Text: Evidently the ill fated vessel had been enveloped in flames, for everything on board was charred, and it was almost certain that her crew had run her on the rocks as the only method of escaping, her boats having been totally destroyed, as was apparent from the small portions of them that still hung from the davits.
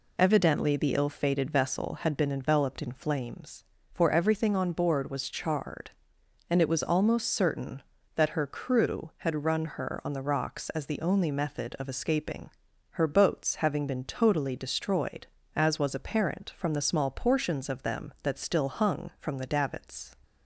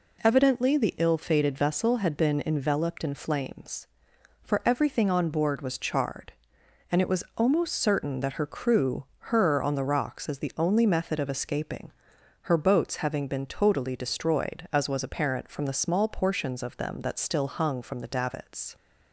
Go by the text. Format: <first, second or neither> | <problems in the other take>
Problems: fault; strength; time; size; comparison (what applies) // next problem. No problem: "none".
first | skips "had run"; at 9.1 s